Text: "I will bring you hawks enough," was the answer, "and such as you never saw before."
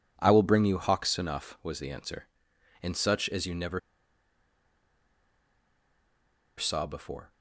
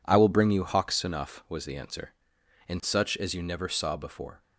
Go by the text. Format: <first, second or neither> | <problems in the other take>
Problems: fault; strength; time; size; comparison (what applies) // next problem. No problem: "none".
second | pauses between "never" and "saw"; strong; at 3.7 s; 2.7 s long